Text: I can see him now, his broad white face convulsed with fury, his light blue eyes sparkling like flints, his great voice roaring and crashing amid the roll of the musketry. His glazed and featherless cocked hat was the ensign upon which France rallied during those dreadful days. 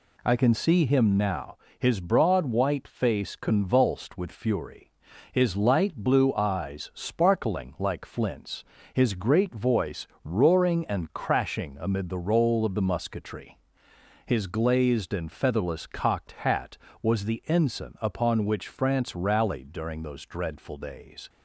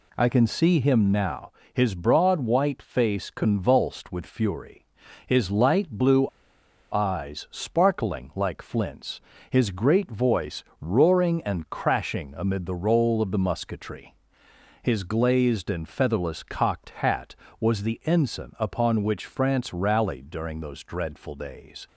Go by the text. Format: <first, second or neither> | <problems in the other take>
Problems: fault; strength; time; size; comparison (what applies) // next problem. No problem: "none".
first | pauses between "blue" and "eyes"; noticeable; at 6.2 s; 0.64 s long // pauses between "voice" and "roaring"; slight; at 10.6 s; 0.18 s long; slight in the first